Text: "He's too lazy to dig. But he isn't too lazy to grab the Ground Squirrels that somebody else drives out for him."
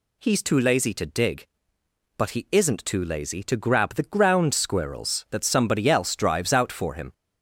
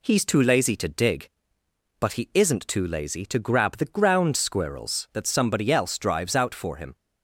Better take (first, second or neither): second